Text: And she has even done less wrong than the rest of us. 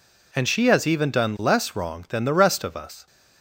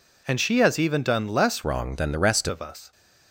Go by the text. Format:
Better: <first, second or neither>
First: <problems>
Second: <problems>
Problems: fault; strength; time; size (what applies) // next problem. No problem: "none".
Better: first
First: none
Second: changes voice from "wrong" to "rest"; from 1.6 to 2.4 s; 0.8 s long